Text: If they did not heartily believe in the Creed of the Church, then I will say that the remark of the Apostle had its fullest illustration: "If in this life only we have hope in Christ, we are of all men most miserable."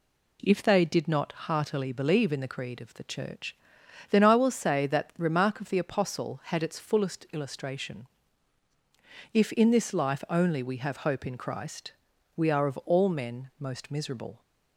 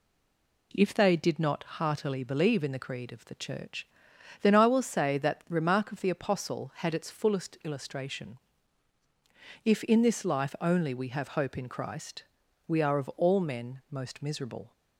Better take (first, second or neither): first